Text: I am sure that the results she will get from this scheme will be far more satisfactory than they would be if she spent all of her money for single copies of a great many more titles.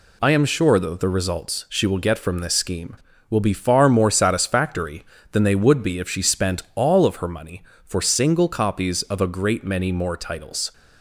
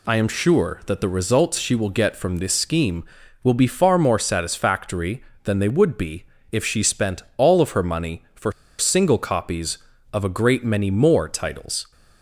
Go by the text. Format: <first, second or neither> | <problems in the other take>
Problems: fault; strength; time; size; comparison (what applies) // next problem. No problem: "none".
first | pauses between "be" and "if"; slight; at 6.2 s; 0.26 s long // pauses between "spent" and "all"; slight; at 7.2 s; 0.16 s long // pauses between "for" and "single"; slight; at 8.5 s; 0.26 s long